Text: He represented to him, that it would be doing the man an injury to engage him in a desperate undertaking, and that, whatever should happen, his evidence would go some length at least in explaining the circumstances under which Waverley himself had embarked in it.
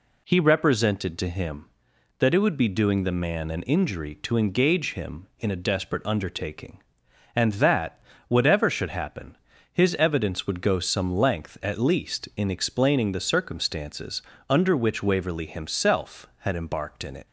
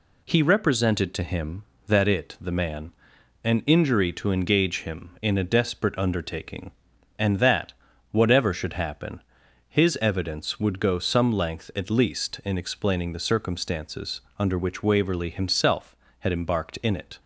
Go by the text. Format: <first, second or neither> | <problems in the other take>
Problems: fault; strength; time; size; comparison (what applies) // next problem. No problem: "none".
first | skips "would be doing"; at 2.3 s // pauses between "man" and "an"; noticeable; at 2.9 s; 0.50 s long // pauses between "circumstances" and "under"; slight; at 14.2 s; 0.18 s long; slight in the first